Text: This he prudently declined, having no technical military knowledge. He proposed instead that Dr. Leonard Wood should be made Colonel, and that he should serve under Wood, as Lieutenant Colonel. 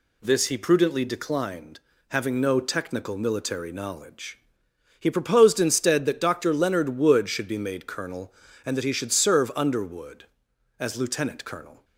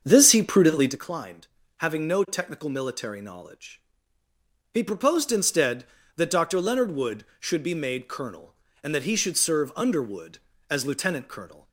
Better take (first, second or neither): first